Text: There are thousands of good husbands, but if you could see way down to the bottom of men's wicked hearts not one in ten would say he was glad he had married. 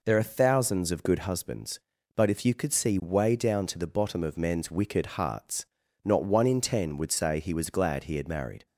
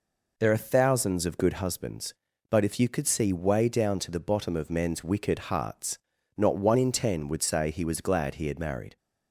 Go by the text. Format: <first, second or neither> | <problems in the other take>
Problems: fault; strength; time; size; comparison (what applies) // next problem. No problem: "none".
neither | pauses between "hearts" and "not"; the same in both